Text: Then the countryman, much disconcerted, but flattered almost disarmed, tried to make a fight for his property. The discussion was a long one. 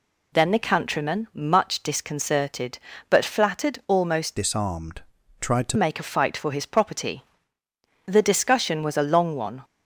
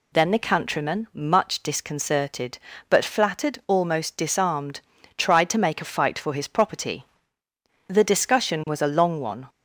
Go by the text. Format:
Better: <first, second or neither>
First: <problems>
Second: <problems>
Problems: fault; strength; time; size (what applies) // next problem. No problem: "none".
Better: second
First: changes voice from "disarmed" to "to"; from 4.3 to 5.7 s; 1.4 s long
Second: none